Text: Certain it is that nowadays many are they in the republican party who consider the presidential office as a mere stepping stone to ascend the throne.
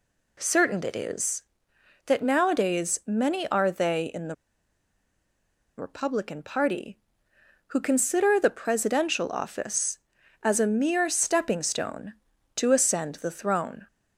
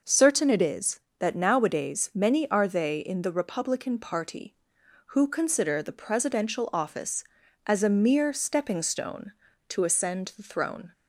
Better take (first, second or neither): second